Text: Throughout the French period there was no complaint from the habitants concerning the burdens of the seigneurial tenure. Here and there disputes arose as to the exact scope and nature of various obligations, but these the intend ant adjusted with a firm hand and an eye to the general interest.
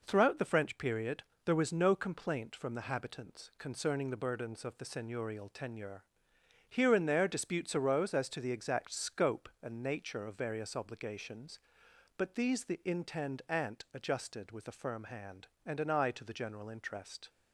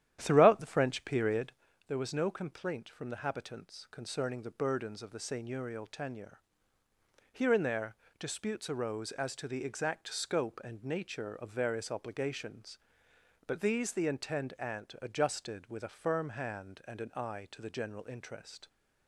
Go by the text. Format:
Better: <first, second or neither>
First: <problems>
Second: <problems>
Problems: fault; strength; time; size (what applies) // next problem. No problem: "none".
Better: first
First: pauses between "period" and "there"; slight; at 1.2 s; 0.22 s long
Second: starts louder than the rest; strong; until 1.7 s; 11 dB // pauses between "period" and "there"; slight; at 1.5 s; 0.34 s long // pauses between "there" and "disputes"; slight; at 7.9 s; 0.24 s long